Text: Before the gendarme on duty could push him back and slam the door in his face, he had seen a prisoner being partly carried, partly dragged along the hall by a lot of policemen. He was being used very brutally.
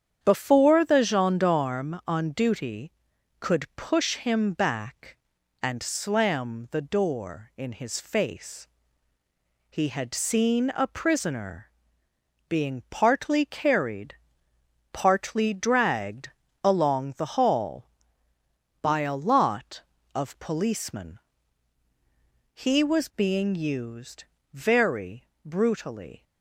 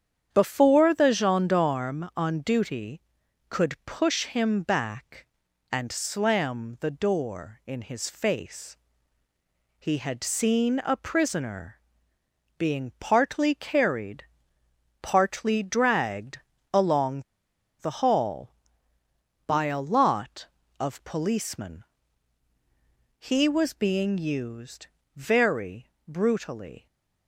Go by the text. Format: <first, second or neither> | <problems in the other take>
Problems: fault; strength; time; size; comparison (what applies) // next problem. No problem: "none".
first | starts louder than the rest; strong; until 1.3 s; 8.5 dB; strong in the first // pauses between "prisoner" and "being"; noticeable; at 11.8 s; 0.78 s long; noticeable in the first // pauses between "dragged" and "along"; slight; at 16.3 s; 0.34 s long; slight in the first // pauses between "along" and "the"; noticeable; at 17.2 s; 0.58 s long // pauses between "used" and "very"; slight; at 24.8 s; 0.30 s long; slight in the first // pauses between "very" and "brutally"; slight; at 25.8 s; 0.18 s long; slight in the first